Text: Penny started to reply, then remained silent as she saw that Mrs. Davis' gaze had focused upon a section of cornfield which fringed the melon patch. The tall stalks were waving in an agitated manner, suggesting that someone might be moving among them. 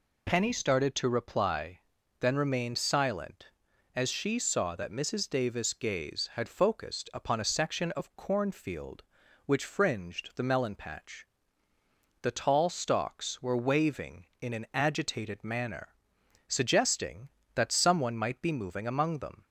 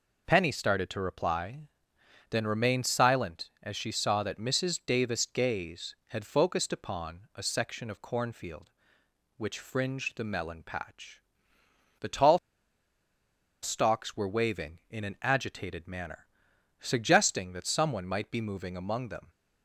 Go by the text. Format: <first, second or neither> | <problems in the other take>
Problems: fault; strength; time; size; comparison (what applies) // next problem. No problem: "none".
first | pauses between "tall" and "stalks"; at 12.3 s; 1.2 s long